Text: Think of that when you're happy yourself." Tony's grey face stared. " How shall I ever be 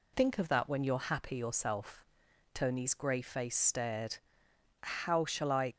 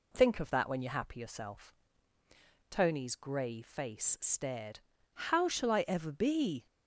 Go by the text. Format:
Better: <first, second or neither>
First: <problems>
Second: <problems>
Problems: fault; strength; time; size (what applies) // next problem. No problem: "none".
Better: second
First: stops before "ever be"; at 5.7 s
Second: none